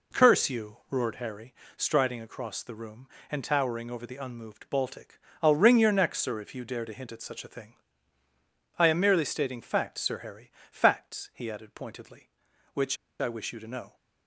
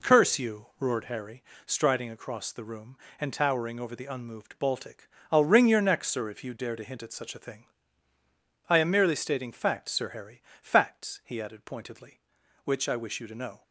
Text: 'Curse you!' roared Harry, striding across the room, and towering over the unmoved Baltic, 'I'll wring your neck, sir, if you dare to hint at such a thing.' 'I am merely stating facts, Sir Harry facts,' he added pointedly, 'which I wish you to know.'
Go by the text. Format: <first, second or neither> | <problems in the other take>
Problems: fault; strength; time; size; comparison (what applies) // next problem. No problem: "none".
second | pauses between "Harry" and "facts"; slight; at 10.5 s; 0.18 s long; slight in the second // pauses between "which" and "I"; slight; at 12.9 s; 0.24 s long